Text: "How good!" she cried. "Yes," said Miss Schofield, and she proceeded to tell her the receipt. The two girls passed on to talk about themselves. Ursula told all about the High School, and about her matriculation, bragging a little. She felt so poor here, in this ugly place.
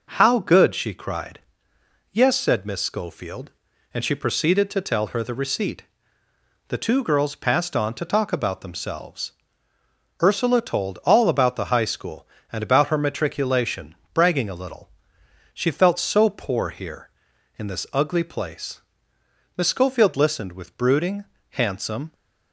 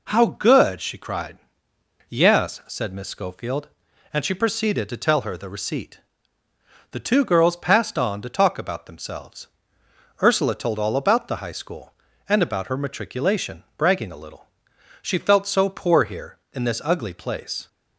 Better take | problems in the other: second | goes on to say "Miss Schofield listened with brooding handsome"; strong; from 19.5 s on; 2.5 s long

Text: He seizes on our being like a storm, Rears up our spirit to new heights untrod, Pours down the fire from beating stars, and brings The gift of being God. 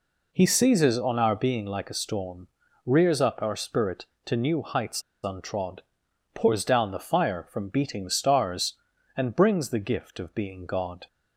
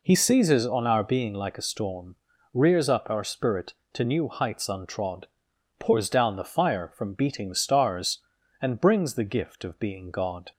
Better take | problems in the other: second | pauses between "heights" and "untrod"; slight; at 5.0 s; 0.21 s long

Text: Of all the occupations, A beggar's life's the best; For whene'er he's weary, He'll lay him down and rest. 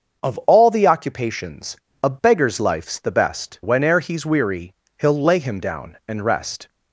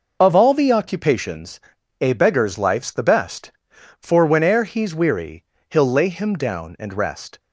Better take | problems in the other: second | starts louder than the rest; until 1.2 s; 6.5 dB // skips "For"; at 3.6 s

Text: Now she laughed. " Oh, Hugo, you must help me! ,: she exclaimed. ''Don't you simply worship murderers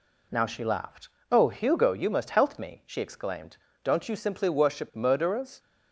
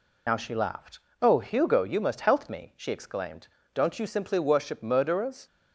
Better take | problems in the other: first | loses the start of "Now"; at 0.2 s; 55 ms

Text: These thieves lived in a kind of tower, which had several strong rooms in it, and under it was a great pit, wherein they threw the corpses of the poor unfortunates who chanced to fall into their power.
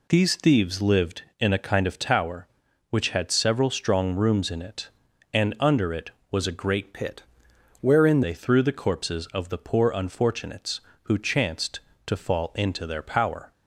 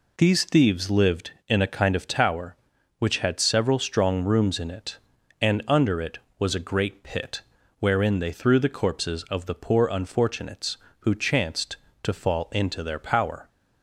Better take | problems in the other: second | changes voice from "pit" to "wherein"; from 6.9 to 8.2 s; 1.3 s long

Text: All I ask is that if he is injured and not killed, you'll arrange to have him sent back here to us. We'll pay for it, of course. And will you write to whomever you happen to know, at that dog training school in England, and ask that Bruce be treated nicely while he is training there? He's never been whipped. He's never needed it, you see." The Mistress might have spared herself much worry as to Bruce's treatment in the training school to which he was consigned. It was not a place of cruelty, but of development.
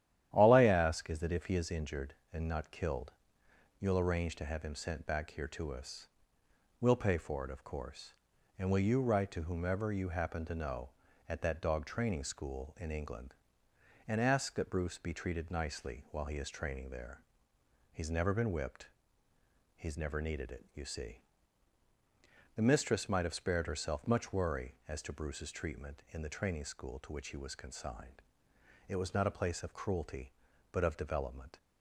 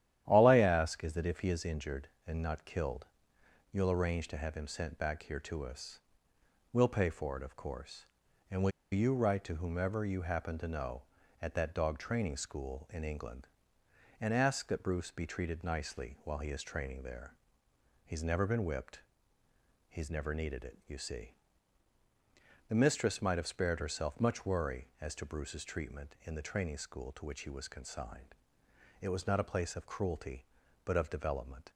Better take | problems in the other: first | starts louder than the rest; strong; until 1.2 s; 11.5 dB; strong in the first // pauses between "will" and "you"; slight; at 8.7 s; 0.20 s long

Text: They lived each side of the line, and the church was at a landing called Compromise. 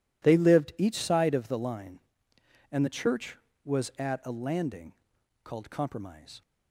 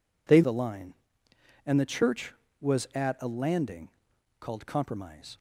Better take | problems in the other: first | skips "lived each side of"; at 0.4 s // pauses between "landing" and "called"; noticeable; at 3.8 s; 0.50 s long; noticeable in the first

